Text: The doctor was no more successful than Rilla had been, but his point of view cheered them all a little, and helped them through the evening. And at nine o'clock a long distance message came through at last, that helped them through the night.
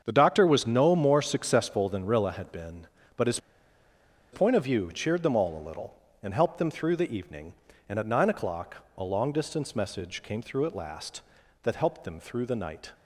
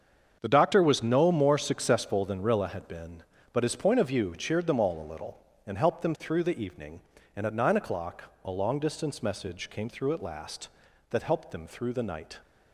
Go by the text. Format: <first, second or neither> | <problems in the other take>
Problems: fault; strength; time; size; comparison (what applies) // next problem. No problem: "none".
second | starts louder than the rest; until 1.0 s; 7 dB; also in the second // pauses between "his" and "point"; noticeable; at 3.3 s; 0.94 s long // pauses between "o'clock" and "a"; slight; at 8.7 s; 0.20 s long; slight in the second